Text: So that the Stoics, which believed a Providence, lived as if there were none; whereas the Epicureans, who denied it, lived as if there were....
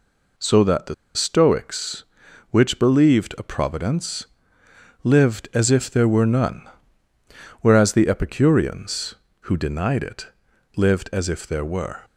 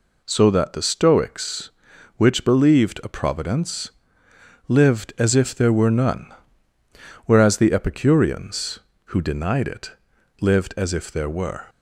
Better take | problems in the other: second | pauses between "the" and "Stoics"; slight; at 0.9 s; 0.22 s long

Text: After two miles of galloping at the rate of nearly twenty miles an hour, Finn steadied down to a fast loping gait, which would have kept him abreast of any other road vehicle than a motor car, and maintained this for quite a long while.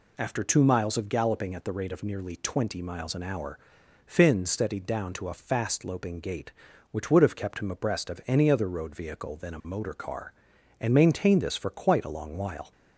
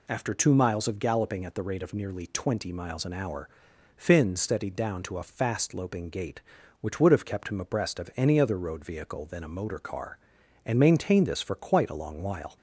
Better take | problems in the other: neither | none

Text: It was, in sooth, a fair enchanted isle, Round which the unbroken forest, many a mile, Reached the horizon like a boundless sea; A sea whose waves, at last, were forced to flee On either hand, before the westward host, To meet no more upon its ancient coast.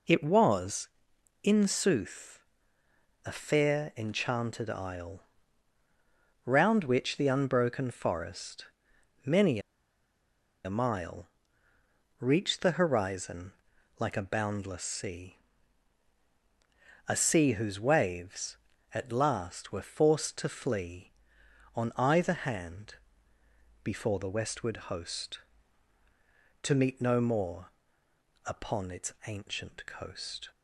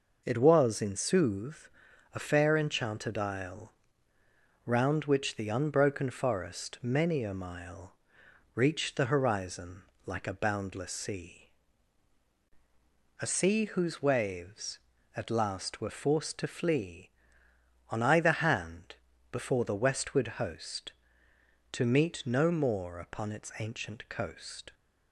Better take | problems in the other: second | pauses between "many" and "a"; at 9.5 s; 1.0 s long // pauses between "horizon" and "like"; noticeable; at 13.5 s; 0.46 s long; slight in the second // pauses between "more" and "upon"; noticeable; at 27.6 s; 0.78 s long

